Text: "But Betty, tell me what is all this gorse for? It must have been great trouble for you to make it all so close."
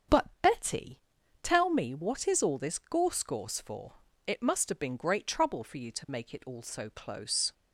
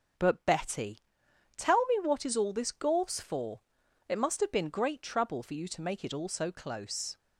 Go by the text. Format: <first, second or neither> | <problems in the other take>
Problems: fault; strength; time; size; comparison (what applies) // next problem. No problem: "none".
second | starts louder than the rest; strong; until 1.7 s; 7.5 dB; also in the second // says "gorse" twice; at 3.2 s